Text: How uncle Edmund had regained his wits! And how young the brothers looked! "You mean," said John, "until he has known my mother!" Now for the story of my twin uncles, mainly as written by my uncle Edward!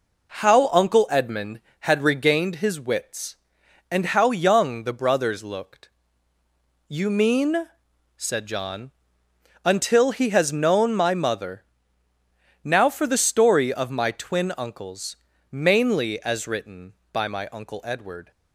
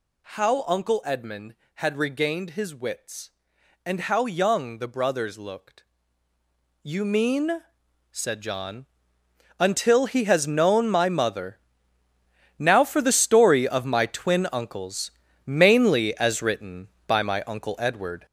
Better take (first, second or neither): first